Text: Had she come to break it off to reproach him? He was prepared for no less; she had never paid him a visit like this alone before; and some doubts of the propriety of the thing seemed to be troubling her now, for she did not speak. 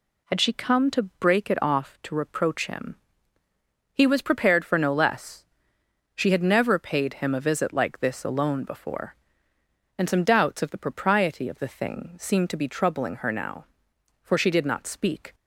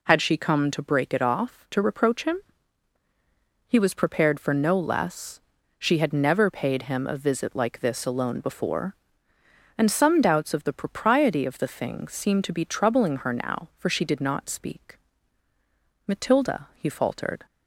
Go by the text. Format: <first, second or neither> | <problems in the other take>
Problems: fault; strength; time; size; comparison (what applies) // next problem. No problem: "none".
first | goes on to say "Matilda he faltered"; from 16.0 s on; 1.4 s long